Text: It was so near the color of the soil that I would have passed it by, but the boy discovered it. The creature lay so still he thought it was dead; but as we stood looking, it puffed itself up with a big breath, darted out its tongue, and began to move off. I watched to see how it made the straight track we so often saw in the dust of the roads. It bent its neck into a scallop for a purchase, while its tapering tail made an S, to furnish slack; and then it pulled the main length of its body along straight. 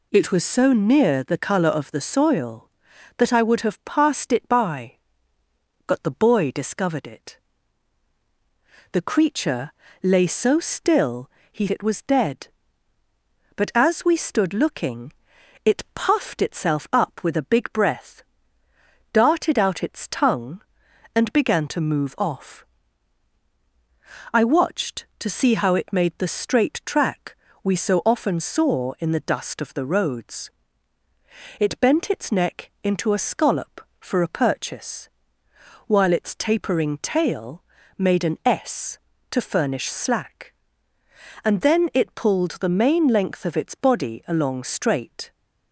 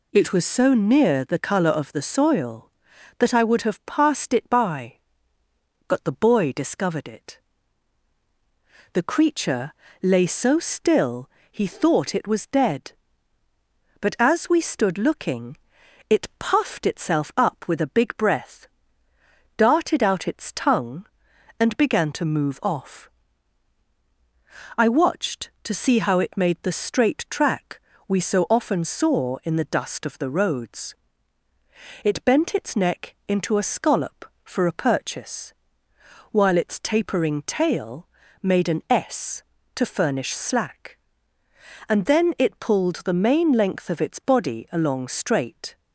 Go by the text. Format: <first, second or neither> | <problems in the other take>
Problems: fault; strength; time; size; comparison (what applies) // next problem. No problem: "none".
second | pauses between "creature" and "lay"; slight; at 9.7 s; 0.30 s long; slight in the second // pauses between "still" and "he"; slight; at 11.2 s; 0.22 s long; slight in the second // skips "thought"; at 11.6 s // pauses between "track" and "we"; slight; at 27.3 s; 0.28 s long; slight in the second // pauses between "tail" and "made"; slight; at 37.6 s; 0.34 s long; slight in the second